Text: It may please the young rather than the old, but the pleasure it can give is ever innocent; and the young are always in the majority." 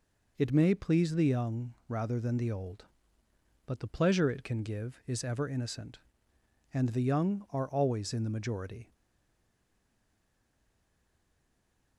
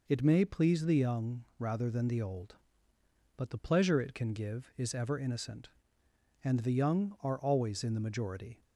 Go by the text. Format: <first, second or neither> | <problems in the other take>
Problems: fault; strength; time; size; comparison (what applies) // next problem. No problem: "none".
second | stays silent after the last word; strong; from 8.9 s on; 3.0 s long